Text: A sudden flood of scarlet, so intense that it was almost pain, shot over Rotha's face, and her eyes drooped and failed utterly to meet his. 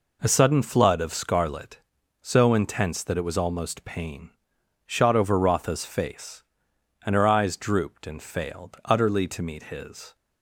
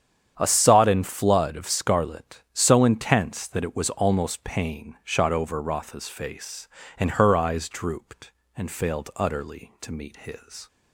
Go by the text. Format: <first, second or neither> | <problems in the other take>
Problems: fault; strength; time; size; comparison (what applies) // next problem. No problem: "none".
first | starts louder than the rest; strong; until 1.3 s; 8.5 dB // says "sodden" for "sudden"; at 0.4 s